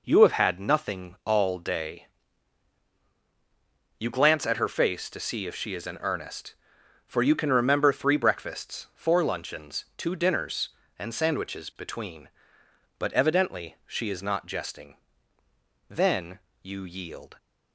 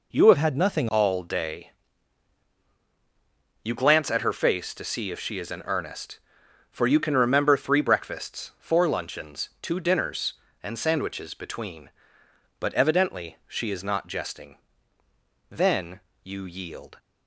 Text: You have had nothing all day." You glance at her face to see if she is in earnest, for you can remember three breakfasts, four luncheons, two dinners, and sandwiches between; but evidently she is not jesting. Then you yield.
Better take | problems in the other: first | changes voice from "had" to "nothing"; from 0.3 to 0.8 s; 0.5 s long // pauses between "Then" and "you"; slight; at 16.0 s; 0.22 s long; slight in the first

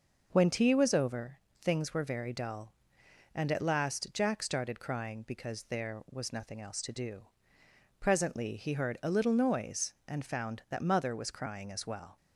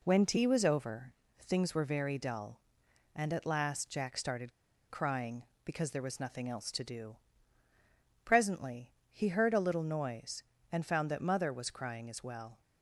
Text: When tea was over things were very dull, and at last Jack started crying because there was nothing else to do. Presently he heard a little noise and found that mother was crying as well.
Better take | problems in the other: first | pauses between "over" and "things"; slight; at 1.1 s; 0.26 s long; slight in the first // pauses between "started" and "crying"; at 4.5 s; 0.39 s long // pauses between "Presently" and "he"; slight; at 8.9 s; 0.20 s long

